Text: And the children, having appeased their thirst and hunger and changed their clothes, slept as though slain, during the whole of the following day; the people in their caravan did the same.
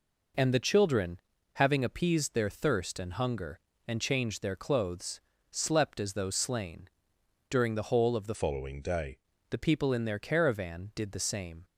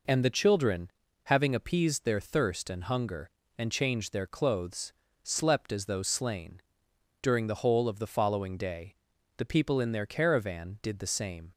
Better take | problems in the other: second | changes voice from "following" to "day"; from 8.3 to 9.1 s; 0.8 s long

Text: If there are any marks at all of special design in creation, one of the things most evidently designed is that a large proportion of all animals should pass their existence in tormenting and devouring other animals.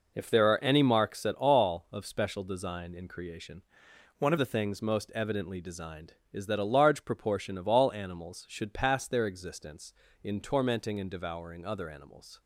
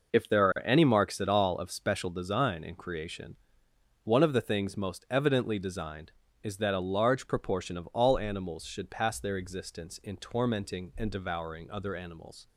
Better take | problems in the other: second | changes voice from "one" to "of"; from 4.1 to 4.3 s; 0.2 s long

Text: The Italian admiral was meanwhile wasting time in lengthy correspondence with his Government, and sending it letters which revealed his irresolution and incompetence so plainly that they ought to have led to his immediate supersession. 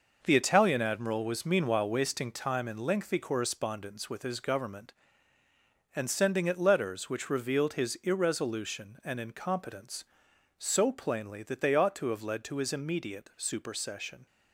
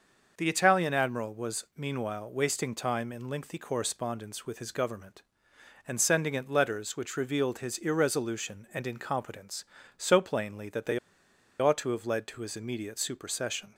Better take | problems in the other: first | starts louder than the rest; noticeable; until 1.4 s; 6 dB // pauses between "they" and "ought"; noticeable; at 10.9 s; 0.62 s long

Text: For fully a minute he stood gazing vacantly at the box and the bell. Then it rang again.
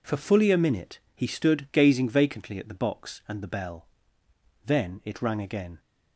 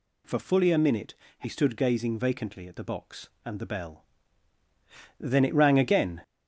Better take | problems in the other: first | gets louder; noticeable; throughout; 4 dB // pauses between "minute" and "he"; slight; at 1.1 s; 0.24 s long; slight in the first

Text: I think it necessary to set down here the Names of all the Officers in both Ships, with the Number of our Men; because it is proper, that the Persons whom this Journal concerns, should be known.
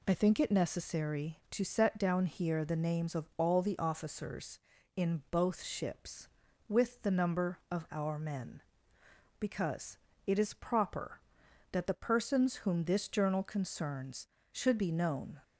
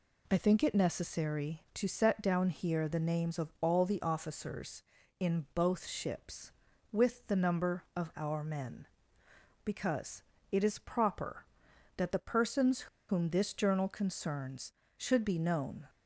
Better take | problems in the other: first | pauses between "because" and "it"; slight; at 10.2 s; 0.26 s long; slight in the first // pauses between "Persons" and "whom"; slight; at 12.8 s; 0.22 s long

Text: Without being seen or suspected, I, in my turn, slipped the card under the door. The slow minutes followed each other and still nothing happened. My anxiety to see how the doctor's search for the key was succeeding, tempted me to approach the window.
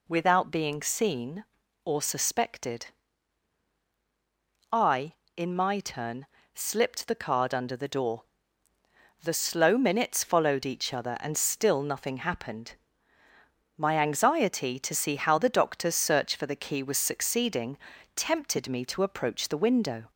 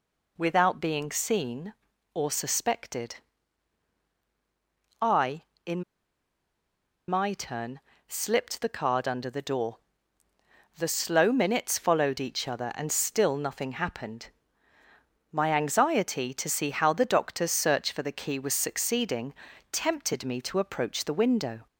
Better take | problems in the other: first | pauses between "in" and "my"; strong; at 5.8 s; 1.2 s long

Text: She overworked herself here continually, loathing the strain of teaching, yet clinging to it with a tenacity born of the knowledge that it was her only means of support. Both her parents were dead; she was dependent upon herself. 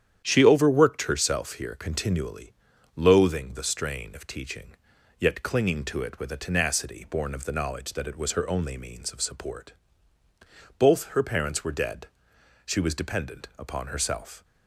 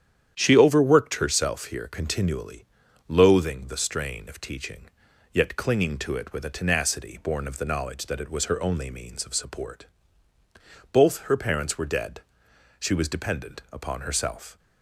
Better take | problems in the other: neither | starts louder than the rest; strong; the same in both

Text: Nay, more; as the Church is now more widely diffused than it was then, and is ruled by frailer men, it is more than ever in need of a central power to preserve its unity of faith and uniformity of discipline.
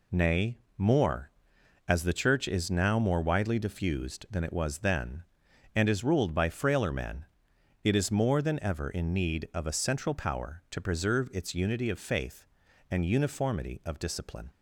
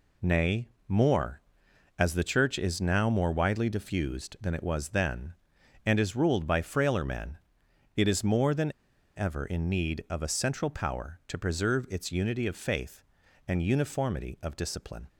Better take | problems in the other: first | pauses between "than" and "ever"; noticeable; at 8.7 s; 0.46 s long

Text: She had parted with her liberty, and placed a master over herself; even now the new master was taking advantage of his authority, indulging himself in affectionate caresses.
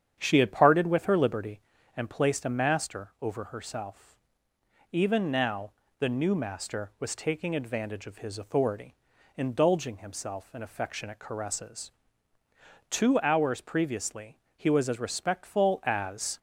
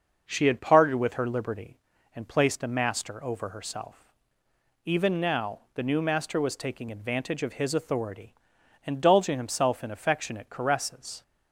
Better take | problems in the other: second | starts louder than the rest; strong; until 1.1 s; 8.5 dB; noticeable in the second // pauses between "now" and "the"; slight; at 5.7 s; 0.28 s long // goes on to say "Two hours previously he was as respectful as"; strong; from 12.8 s on; 3.5 s long

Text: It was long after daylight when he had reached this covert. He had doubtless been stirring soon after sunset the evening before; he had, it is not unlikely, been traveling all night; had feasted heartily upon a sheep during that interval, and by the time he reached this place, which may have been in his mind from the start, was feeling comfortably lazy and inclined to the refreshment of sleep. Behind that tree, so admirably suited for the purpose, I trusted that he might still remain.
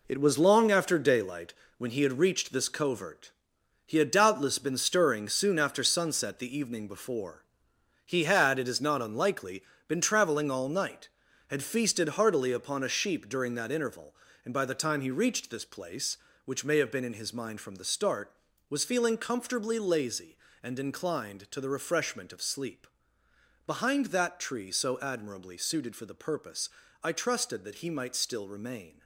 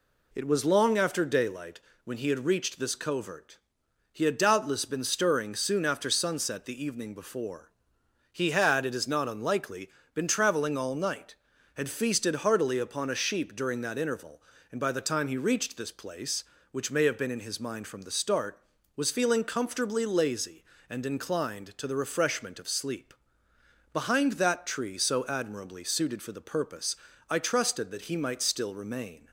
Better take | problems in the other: second | gets quieter; strong; throughout; 8.5 dB // pauses between "daylight" and "when"; slight; at 1.5 s; 0.24 s long; slight in the second

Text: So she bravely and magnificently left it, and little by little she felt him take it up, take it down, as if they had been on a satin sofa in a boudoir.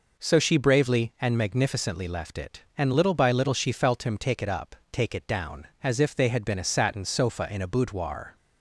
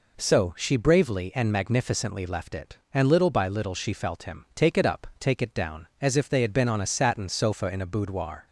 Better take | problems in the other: second | skips "on"; at 6.5 s

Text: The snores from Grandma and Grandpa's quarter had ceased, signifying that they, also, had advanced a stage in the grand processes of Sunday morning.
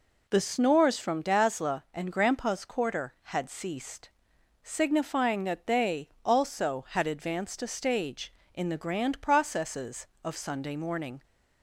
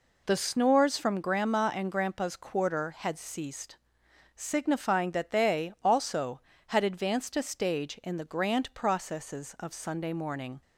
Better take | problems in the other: second | says "Dazzla" for "Grandma"; at 1.2 s

